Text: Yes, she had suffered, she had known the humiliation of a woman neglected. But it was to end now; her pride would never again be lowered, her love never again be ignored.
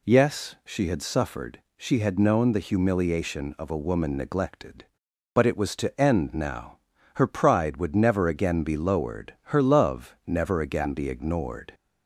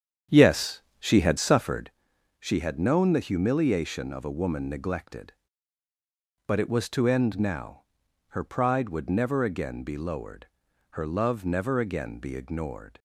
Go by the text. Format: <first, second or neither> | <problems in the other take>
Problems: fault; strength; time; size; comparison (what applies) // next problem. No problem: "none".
first | starts louder than the rest; strong; until 2.0 s; 8.5 dB